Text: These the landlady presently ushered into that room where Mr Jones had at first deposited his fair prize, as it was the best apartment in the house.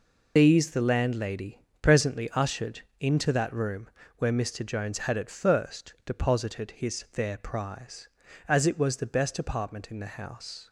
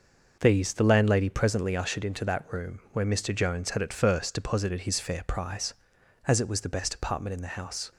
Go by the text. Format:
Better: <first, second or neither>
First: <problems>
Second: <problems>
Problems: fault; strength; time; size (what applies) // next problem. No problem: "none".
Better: second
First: loses the start of "These"; at 0.3 s; 30 ms // pauses between "landlady" and "presently"; slight; at 1.6 s; 0.20 s long // pauses between "ushered" and "into"; slight; at 2.8 s; 0.18 s long // pauses between "room" and "where"; slight; at 3.8 s; 0.28 s long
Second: none